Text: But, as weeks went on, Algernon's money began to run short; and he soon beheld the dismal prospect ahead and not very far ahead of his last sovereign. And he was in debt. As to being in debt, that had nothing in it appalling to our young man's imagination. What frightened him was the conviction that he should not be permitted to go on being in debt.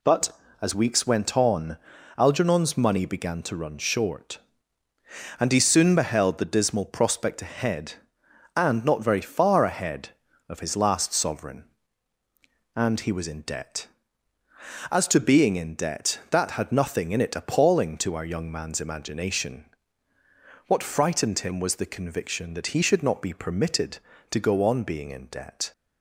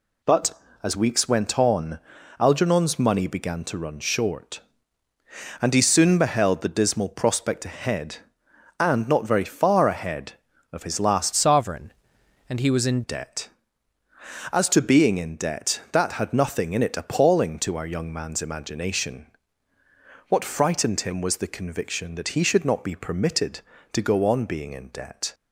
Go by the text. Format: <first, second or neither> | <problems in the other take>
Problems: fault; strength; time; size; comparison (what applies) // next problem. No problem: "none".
first | changes voice from "sovereign" to "in"; from 11.3 to 13.0 s; 1.7 s long